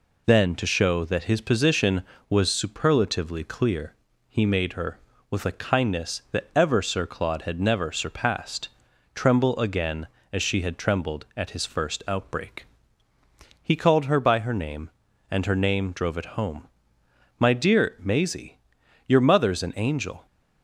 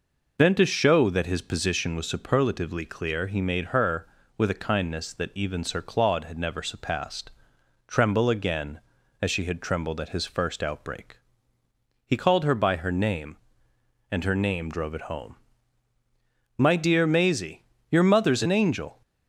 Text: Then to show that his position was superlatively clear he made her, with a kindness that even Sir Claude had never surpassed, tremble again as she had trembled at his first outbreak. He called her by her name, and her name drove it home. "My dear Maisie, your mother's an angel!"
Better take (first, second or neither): second